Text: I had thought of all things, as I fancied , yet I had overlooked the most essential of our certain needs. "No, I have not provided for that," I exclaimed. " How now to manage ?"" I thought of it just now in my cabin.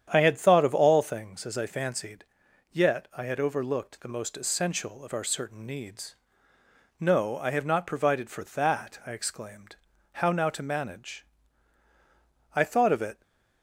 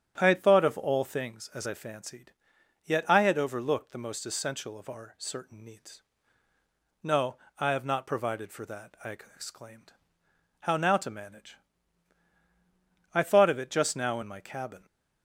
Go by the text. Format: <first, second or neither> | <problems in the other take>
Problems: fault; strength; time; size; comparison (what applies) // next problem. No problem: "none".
second | starts louder than the rest; strong; until 1.1 s; 9 dB; strong in the second // stops before "just now in my cabin"; at 13.2 s